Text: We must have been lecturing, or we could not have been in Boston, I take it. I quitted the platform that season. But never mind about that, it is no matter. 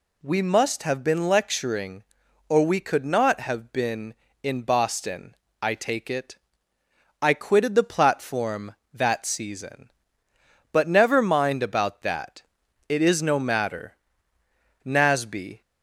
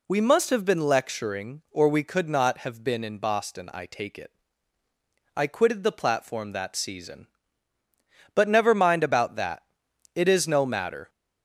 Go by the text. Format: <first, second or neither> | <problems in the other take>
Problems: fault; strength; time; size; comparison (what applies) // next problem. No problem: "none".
second | goes on to say "Nasby"; noticeable; from 14.8 s on; 0.76 s long